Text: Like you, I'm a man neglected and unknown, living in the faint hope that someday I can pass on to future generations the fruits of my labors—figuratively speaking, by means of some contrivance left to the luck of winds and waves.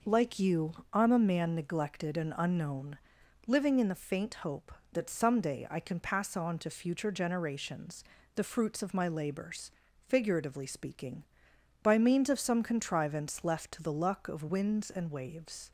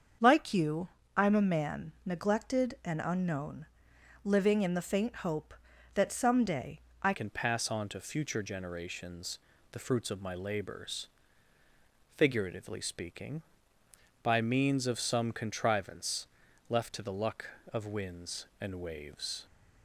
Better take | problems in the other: first | starts louder than the rest; until 1.5 s; 7 dB // pauses between "someday" and "I"; slight; at 6.7 s; 0.24 s long // changes voice at "can"; from 7.1 s on; 12.3 s long // pauses between "generations" and "the"; slight; at 9.3 s; 0.32 s long; slight in the first // pauses between "contrivance" and "left"; at 16.2 s; 0.40 s long

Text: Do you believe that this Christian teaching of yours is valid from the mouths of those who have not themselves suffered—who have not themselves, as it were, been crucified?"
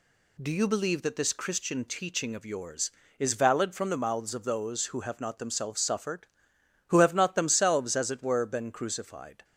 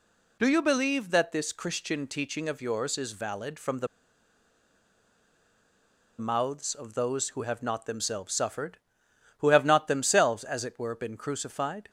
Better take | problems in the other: first | pauses between "the" and "mouths"; strong; at 3.8 s; 2.3 s long

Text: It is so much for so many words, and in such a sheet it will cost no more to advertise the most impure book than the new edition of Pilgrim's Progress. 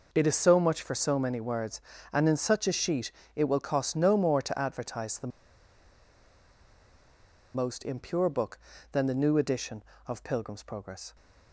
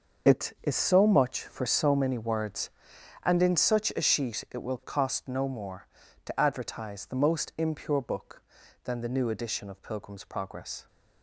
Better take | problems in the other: second | pauses between "sheet" and "it"; slight; at 3.1 s; 0.22 s long // pauses between "the" and "most"; strong; at 5.3 s; 2.2 s long

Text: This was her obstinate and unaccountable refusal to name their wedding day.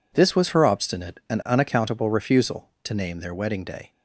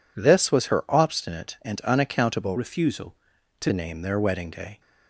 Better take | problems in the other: first | changes voice from "refusal" to "to"; from 2.5 to 3.7 s; 1.2 s long

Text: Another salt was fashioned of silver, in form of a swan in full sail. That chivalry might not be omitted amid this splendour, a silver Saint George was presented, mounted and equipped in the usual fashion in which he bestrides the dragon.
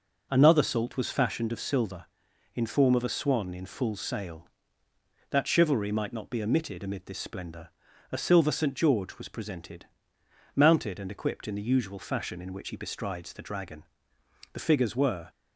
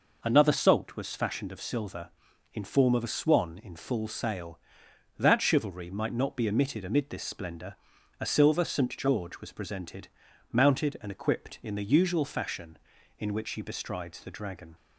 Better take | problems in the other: second | goes on to say "The figures were"; noticeable; from 14.5 s on; 0.76 s long

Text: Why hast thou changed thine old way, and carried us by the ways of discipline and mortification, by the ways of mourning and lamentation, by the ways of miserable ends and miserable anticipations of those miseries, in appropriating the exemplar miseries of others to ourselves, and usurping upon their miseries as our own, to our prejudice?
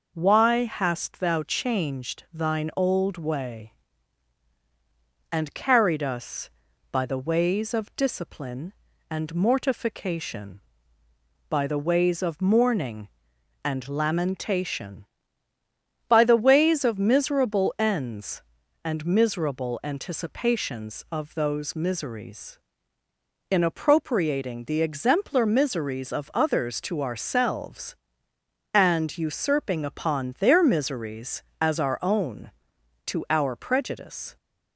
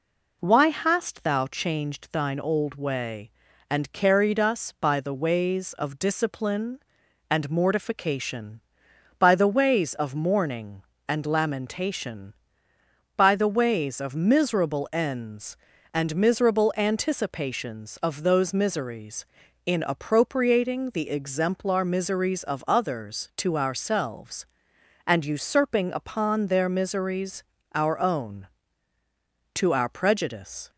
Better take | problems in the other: first | skips "as"; at 27.5 s

